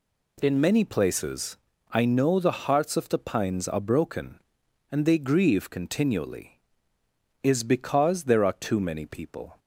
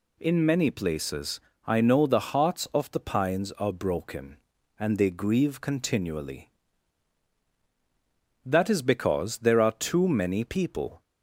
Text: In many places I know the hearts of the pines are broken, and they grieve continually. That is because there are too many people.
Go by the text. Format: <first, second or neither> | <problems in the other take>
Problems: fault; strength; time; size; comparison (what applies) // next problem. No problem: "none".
second | pauses between "places" and "I"; slight; at 1.5 s; 0.34 s long; slight in the second // skips "That"; at 7.0 s